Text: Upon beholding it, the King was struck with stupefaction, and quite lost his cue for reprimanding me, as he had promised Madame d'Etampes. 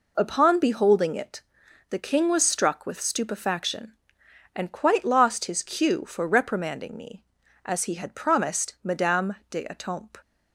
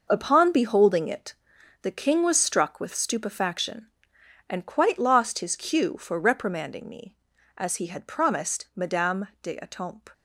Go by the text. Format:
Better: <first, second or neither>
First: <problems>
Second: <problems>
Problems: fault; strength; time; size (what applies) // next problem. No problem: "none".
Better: first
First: none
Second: gets quieter; strong; throughout; 10 dB